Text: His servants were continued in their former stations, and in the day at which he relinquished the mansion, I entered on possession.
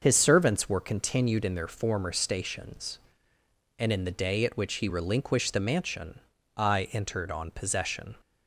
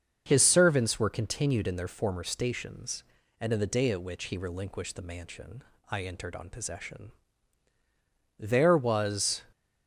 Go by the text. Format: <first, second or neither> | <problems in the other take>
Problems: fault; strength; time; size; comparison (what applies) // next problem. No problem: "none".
first | starts louder than the rest; until 1.2 s; 6.5 dB; also in the first // goes on to say "There was"; noticeable; from 8.4 s on; 1.0 s long